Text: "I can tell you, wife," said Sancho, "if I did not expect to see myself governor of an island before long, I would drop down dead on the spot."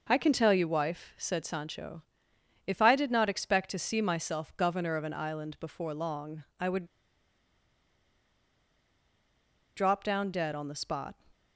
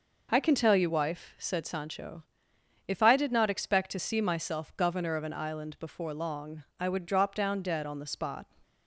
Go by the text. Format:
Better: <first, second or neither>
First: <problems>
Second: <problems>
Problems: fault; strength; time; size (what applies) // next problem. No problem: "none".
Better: second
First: pauses between "would" and "drop"; strong; at 6.8 s; 2.9 s long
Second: none